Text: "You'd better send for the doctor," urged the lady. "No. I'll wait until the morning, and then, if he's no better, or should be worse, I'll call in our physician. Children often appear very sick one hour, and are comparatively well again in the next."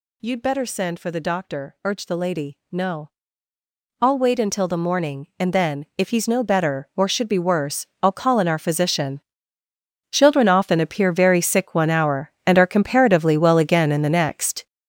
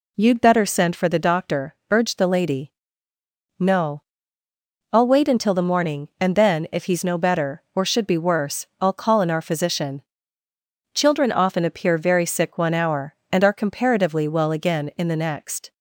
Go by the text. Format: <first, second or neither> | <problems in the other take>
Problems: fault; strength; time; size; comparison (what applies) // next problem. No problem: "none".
second | gets louder; strong; throughout; 9 dB